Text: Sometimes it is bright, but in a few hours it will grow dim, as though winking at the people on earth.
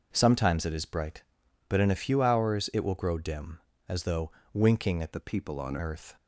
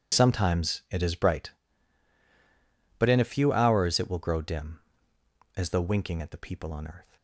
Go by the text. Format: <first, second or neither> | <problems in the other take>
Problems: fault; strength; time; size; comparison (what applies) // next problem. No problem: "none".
second | pauses between "though" and "winking"; slight; at 4.2 s; 0.22 s long // changes voice from "the" to "on"; from 5.1 to 5.7 s; 0.6 s long